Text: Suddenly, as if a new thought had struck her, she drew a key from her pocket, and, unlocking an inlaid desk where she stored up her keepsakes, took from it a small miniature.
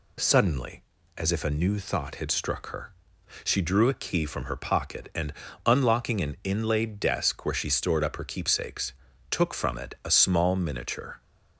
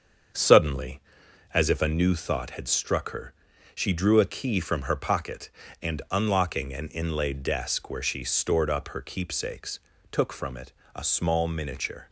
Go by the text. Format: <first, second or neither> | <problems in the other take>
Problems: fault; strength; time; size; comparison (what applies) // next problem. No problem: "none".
first | starts louder than the rest; strong; until 2.1 s; 7.5 dB // pauses between "it" and "a"; slight; at 10.7 s; 0.22 s long